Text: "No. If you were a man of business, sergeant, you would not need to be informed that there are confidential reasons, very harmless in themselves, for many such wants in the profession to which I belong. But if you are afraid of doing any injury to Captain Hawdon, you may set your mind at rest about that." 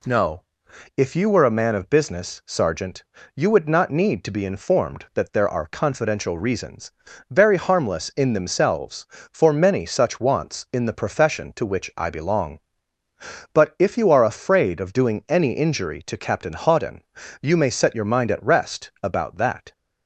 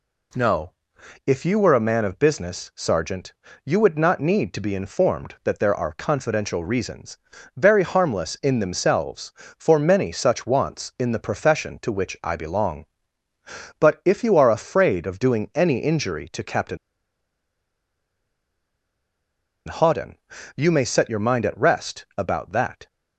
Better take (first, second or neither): first